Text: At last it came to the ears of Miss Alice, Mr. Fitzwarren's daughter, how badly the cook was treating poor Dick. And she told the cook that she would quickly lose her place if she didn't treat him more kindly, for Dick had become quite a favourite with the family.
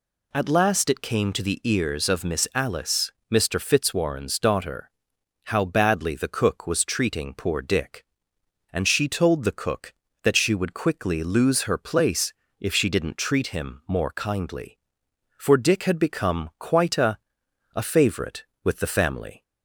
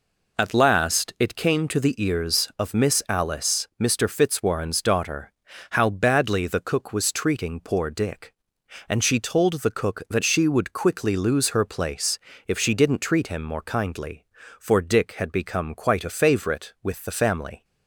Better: second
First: pauses between "place" and "if"; slight; at 12.3 s; 0.28 s long // says "a" twice; at 17.7 s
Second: pauses between "place" and "if"; slight; at 12.1 s; 0.30 s long

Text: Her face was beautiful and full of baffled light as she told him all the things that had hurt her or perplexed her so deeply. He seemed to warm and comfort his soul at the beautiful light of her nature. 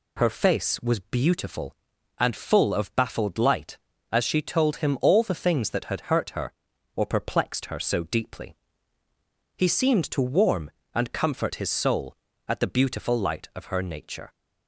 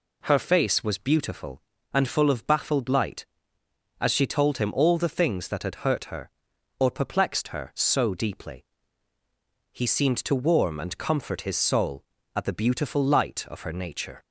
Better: neither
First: none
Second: none

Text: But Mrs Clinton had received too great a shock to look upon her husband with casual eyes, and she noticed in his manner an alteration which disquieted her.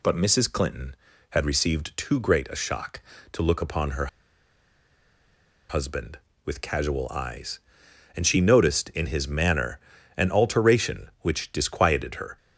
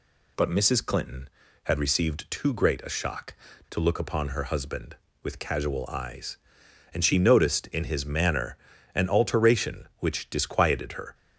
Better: second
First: pauses between "her" and "husband"; strong; at 4.0 s; 1.6 s long // pauses between "manner" and "an"; at 9.7 s; 0.38 s long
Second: pauses between "manner" and "an"; at 8.5 s; 0.38 s long

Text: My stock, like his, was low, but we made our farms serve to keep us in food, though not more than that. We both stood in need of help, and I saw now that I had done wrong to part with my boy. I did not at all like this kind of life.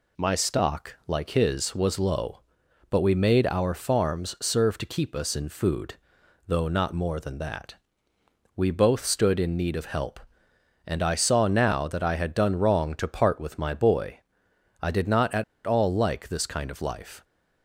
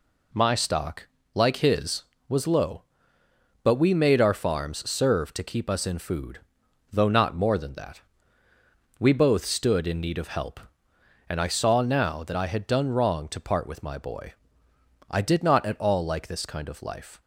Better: second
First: pauses between "at" and "all"; slight; at 15.4 s; 0.23 s long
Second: none

